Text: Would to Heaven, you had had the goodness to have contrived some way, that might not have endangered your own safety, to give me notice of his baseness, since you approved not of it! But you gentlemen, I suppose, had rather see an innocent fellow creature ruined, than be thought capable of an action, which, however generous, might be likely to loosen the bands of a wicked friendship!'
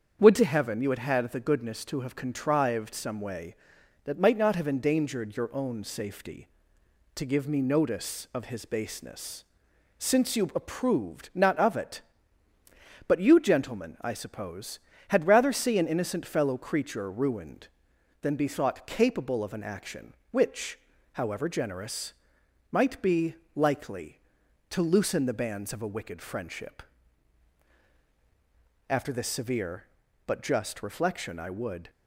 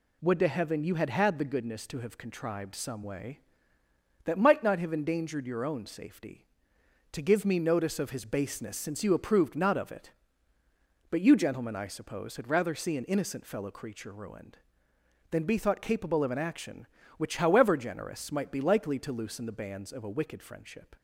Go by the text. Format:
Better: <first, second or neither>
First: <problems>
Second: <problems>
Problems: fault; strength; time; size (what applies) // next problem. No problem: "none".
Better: second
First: starts louder than the rest; strong; until 1.2 s; 7.5 dB // pauses between "be" and "likely"; slight; at 23.3 s; 0.20 s long // goes on to say "After this severe but just reflection I would"; strong; from 28.8 s on; 3.0 s long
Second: none